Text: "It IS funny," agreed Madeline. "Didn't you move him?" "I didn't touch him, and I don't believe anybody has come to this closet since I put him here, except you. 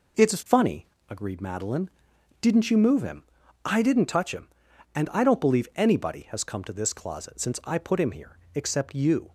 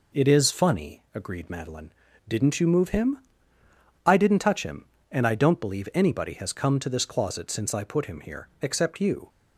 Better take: neither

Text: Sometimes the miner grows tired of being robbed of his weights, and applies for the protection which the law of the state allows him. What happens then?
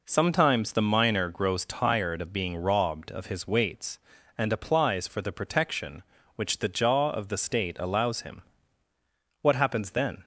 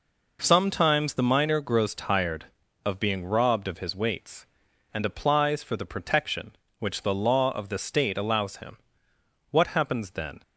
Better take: second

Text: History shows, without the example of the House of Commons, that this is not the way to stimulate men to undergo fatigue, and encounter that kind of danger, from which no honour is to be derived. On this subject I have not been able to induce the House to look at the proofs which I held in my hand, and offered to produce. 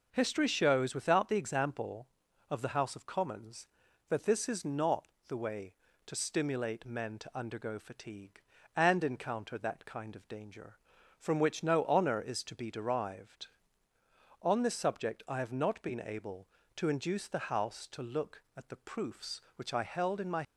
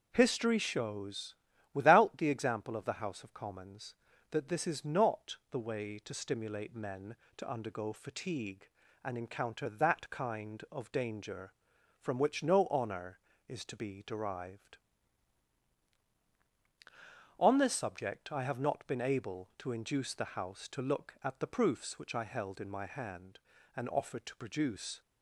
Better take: second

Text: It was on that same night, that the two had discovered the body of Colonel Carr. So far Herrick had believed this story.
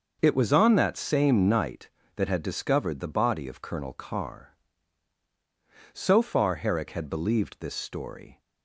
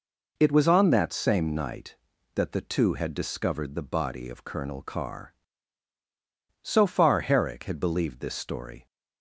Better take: second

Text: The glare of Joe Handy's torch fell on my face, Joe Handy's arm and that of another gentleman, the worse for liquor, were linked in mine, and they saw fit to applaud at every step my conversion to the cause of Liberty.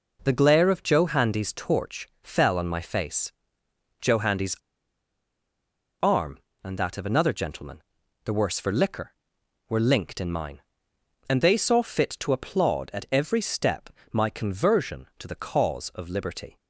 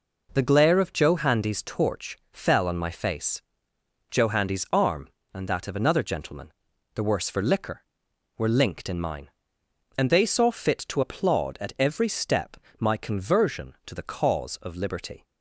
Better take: second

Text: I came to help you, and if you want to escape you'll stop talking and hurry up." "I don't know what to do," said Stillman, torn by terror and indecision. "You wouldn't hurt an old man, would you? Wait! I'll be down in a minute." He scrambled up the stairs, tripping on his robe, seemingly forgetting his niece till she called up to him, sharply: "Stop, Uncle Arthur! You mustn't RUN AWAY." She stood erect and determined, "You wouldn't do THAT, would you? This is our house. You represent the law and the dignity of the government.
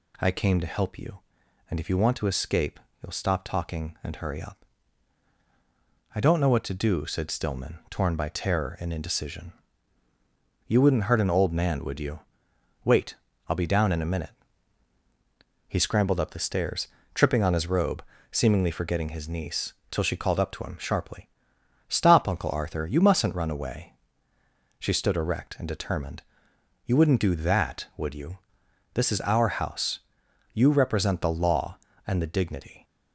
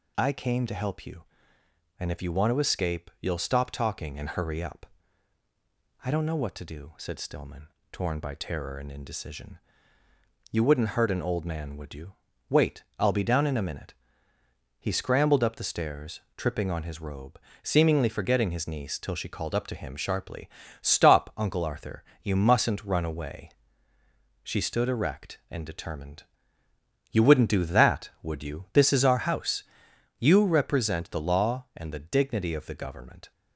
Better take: second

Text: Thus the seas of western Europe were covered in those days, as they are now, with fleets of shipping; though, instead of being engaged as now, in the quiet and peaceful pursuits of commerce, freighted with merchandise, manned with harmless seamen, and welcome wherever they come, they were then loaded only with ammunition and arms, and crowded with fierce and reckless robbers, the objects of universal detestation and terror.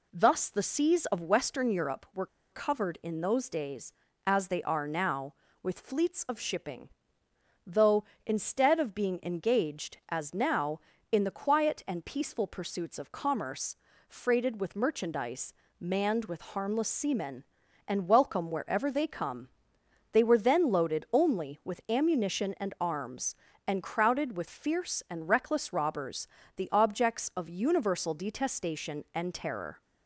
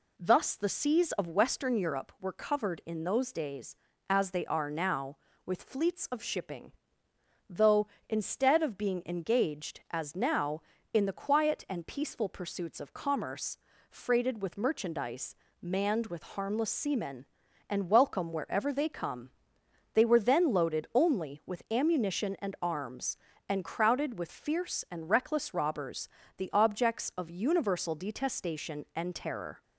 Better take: second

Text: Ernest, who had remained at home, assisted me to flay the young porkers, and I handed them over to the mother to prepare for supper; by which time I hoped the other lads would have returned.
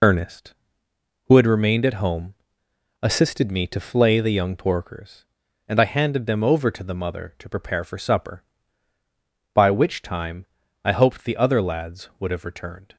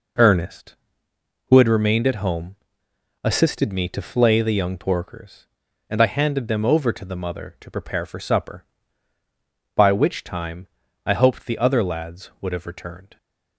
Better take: second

